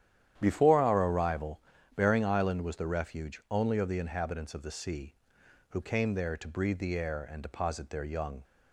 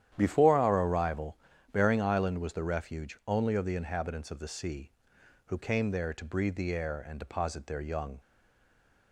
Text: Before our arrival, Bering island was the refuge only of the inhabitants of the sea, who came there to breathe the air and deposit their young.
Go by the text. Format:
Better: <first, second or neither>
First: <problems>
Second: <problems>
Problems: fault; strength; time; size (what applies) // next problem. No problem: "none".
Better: first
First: starts louder than the rest; strong; until 1.3 s; 10.5 dB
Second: starts louder than the rest; strong; until 1.1 s; 10.5 dB // stays silent after the last word; slight; from 8.1 s on; 1.0 s long